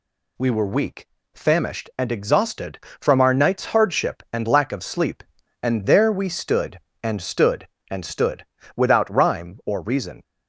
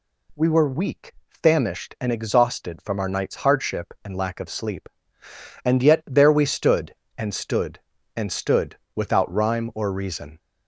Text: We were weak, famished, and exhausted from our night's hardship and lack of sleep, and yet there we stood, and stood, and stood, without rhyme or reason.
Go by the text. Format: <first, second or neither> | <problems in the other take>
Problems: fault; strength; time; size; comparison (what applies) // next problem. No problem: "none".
second | skips "yet"; at 5.8 s